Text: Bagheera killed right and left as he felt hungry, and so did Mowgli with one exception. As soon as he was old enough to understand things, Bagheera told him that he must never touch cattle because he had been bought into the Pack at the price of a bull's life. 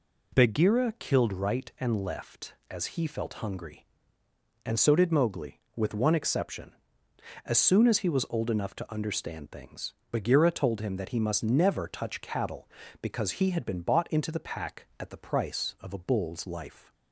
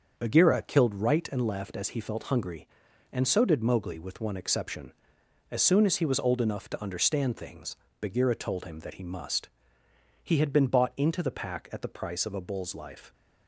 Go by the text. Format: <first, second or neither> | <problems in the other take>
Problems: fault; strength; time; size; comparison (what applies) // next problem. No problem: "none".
first | starts louder than the rest; until 1.1 s; 6.5 dB // skips "never touch cattle because"; at 9.8 s